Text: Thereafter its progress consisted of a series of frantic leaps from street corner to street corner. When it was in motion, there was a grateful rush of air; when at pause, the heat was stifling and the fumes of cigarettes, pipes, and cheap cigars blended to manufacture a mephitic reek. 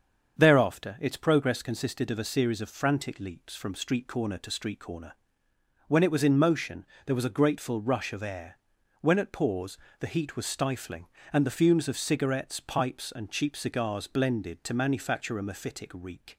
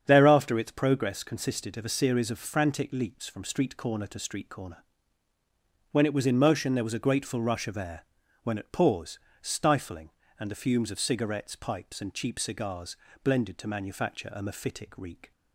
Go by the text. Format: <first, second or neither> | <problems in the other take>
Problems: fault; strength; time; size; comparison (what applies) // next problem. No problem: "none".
first | starts louder than the rest; strong; until 1.0 s; 8 dB; also in the first // skips "the heat was"; at 9.3 s // pauses between "cigars" and "blended"; slight; at 12.9 s; 0.26 s long